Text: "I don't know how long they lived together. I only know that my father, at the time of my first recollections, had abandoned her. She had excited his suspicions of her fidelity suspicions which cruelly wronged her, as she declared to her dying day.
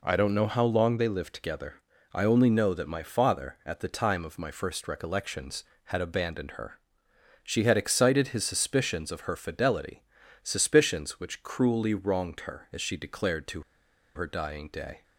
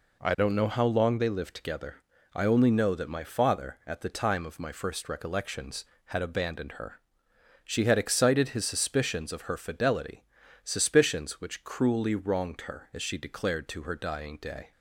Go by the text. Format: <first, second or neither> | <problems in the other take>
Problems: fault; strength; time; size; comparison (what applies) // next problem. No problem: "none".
second | pauses between "fidelity" and "suspicions"; at 10.0 s; 0.40 s long; also in the second // pauses between "to" and "her"; noticeable; at 13.6 s; 0.52 s long